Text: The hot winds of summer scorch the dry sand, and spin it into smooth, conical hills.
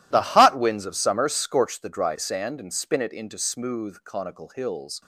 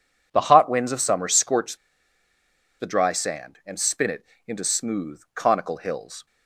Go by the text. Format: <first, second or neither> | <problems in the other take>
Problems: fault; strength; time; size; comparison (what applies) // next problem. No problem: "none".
first | pauses between "scorch" and "the"; at 1.7 s; 1.0 s long // pauses between "it" and "into"; slight; at 4.2 s; 0.20 s long